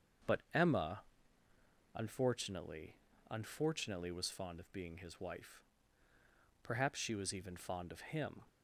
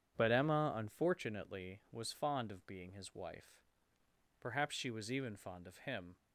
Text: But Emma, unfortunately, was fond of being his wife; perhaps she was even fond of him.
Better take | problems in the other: second | starts louder than the rest; until 2.3 s; 7 dB; strong in the second // says "unfortunately" twice; at 3.3 s

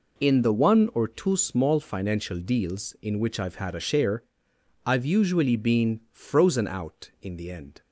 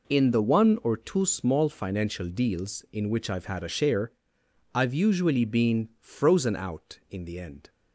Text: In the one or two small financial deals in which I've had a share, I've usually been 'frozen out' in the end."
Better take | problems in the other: neither | none

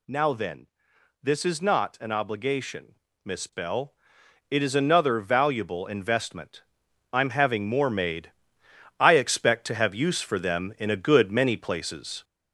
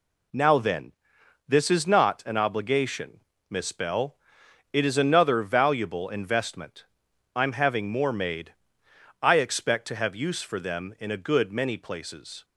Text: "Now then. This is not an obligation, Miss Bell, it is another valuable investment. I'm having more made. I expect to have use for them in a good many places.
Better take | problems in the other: second | gets louder; slight; throughout; 3 dB

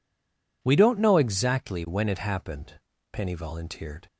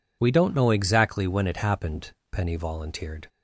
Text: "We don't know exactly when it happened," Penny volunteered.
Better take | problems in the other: second | stays silent before the first word; slight; until 0.6 s; 0.6 s long

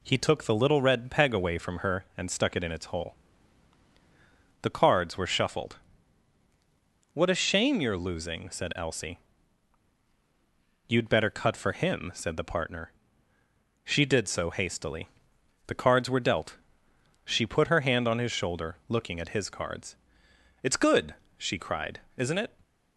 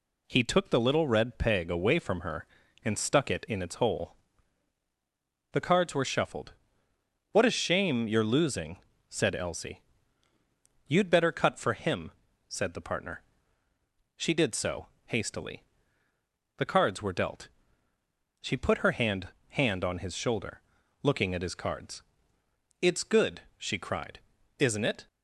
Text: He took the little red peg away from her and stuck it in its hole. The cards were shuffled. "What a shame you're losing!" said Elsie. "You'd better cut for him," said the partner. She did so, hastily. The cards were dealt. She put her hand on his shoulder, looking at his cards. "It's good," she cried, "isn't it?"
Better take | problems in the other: first | says "hand" twice; at 19.4 s

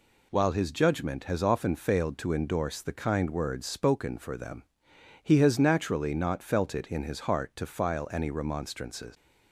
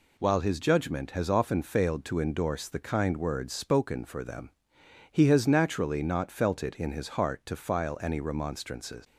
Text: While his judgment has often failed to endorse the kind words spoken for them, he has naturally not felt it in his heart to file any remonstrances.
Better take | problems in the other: neither | none

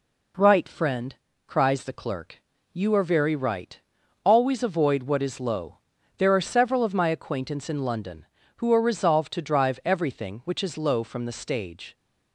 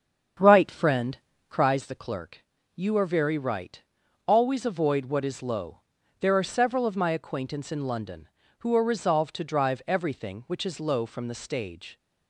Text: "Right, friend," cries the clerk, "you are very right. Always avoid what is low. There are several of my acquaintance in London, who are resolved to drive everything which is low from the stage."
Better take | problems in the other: first | starts louder than the rest; strong; until 1.8 s; 8 dB

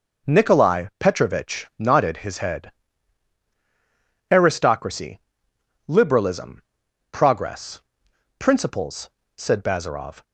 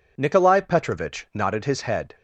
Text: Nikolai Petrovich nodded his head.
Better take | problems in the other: second | goes on to say "Aristocracy liberalism progress principles said Bazarov"; strong; from 4.3 s on; 5.9 s long

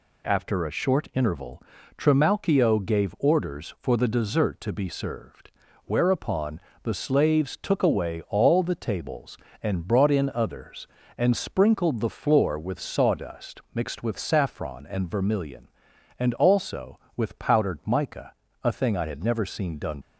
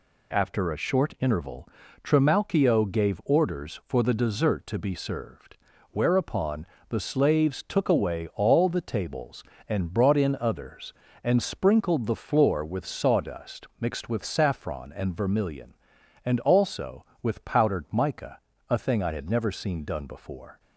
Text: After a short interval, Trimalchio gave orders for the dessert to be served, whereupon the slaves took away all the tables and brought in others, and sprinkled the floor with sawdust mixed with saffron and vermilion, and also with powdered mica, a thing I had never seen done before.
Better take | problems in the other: second | pauses between "whereupon" and "the"; slight; at 6.5 s; 0.22 s long; slight in the second // stops before "before"; at 20.0 s

